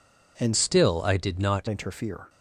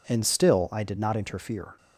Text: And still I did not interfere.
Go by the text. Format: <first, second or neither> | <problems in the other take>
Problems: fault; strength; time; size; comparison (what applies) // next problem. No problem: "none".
second | changes voice from "still" to "not"; from 0.5 to 1.6 s; 1.1 s long